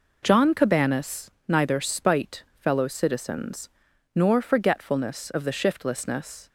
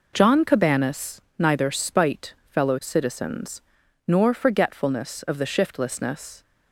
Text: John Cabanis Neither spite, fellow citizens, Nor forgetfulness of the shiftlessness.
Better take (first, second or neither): neither